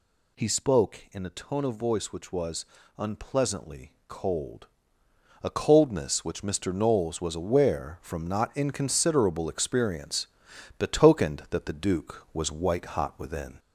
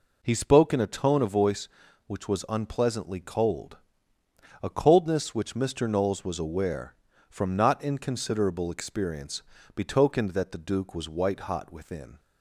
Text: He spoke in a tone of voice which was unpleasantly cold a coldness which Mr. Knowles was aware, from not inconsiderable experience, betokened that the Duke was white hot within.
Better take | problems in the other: second | gets louder; slight; throughout; 2.5 dB // pauses between "was" and "unpleasantly"; slight; at 2.6 s; 0.34 s long // pauses between "unpleasantly" and "cold"; slight; at 3.9 s; 0.16 s long // pauses between "cold" and "a"; noticeable; at 4.6 s; 0.76 s long; noticeable in the second

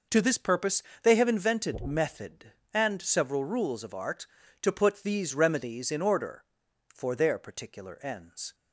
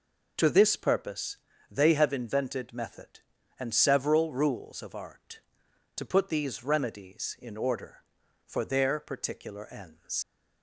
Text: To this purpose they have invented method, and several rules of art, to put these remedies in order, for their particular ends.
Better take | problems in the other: first | pauses between "purpose" and "they"; slight; at 1.3 s; 0.34 s long; slight in the first // leaves "ends" unfinished; at 10.2 s; 115 ms

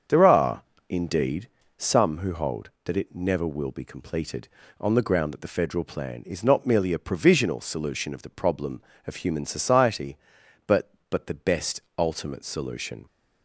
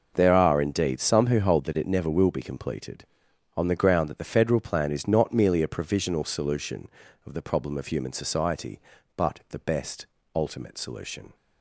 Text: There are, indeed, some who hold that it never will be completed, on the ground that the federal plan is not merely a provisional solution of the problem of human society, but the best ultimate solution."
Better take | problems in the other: second | starts louder than the rest; strong; until 1.3 s; 7.5 dB // says "but" twice; at 11.0 s // pauses between "best" and "ultimate"; slight; at 11.7 s; 0.18 s long; slight in the second

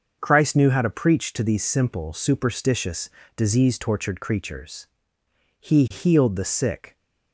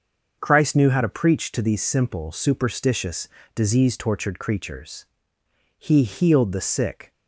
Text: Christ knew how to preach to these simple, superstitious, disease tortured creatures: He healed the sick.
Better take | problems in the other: neither | starts louder than the rest; the same in both

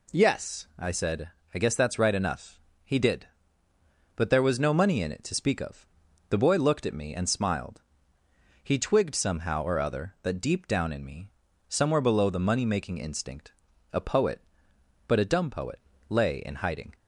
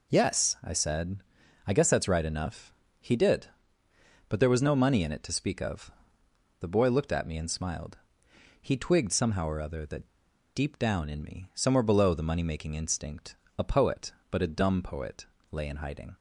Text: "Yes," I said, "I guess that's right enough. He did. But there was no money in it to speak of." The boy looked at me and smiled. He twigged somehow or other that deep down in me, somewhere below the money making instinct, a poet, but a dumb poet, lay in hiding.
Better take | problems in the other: first | pauses between "that" and "deep"; noticeable; at 10.0 s; 0.46 s long

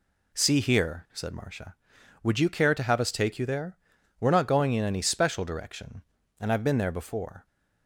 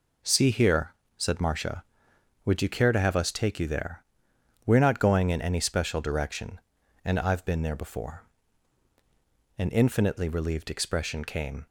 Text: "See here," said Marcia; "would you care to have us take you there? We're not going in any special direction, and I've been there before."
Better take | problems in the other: first | goes on to say "An infinitely relieved expression came"; strong; from 9.5 s on; 2.0 s long

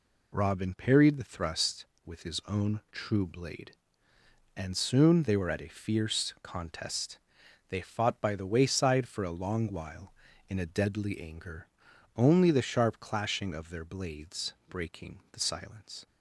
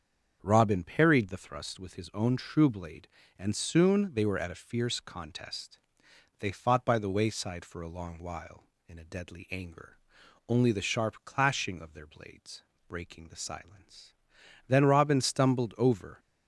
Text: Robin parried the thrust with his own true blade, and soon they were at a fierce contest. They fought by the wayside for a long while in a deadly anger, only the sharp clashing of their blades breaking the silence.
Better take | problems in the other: first | starts louder than the rest; strong; until 1.4 s; 7 dB // pauses between "blades" and "breaking"; slight; at 12.6 s; 0.24 s long; slight in the first // goes on to say "Then Robin stumbled over"; from 14.6 s on; 1.5 s long

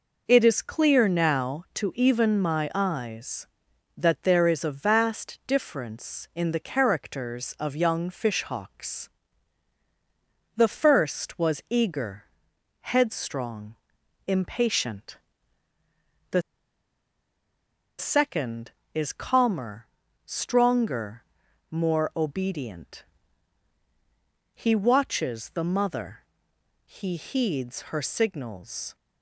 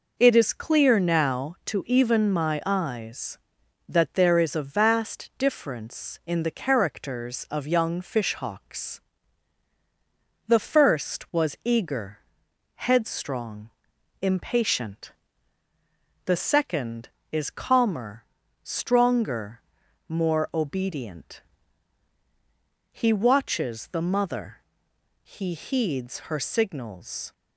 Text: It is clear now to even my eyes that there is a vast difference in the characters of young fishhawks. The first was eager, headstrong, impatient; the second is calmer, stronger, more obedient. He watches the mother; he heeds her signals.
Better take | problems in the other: second | pauses between "the" and "second"; strong; at 16.4 s; 1.5 s long

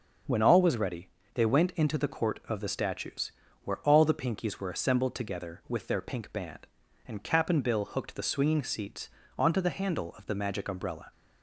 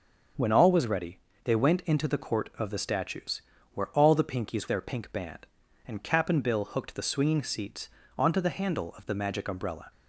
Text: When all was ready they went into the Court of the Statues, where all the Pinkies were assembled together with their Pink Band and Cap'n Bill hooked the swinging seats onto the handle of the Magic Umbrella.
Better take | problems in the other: first | starts louder than the rest; until 1.6 s; 6.5 dB; also in the first // pauses between "ready" and "they"; slight; at 1.1 s; 0.26 s long; slight in the first // skips "were assembled together with"; at 4.6 s // pauses between "seats" and "onto"; slight; at 7.9 s; 0.26 s long; slight in the first

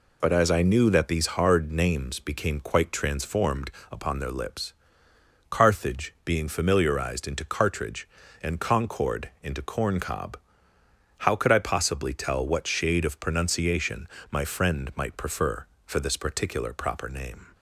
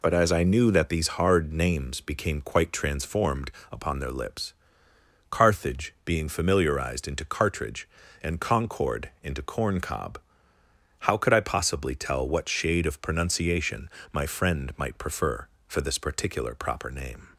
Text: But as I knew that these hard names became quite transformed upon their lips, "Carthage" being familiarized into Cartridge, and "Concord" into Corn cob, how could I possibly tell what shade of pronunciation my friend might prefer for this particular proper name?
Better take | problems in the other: neither | pauses between "transformed" and "upon"; slight; the same in both // pauses between "pronunciation" and "my"; slight; the same in both

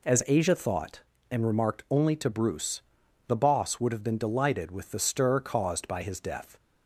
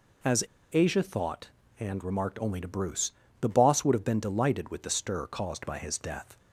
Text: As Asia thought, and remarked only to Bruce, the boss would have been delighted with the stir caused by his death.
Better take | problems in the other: first | pauses between "As" and "Asia"; slight; at 0.4 s; 0.30 s long

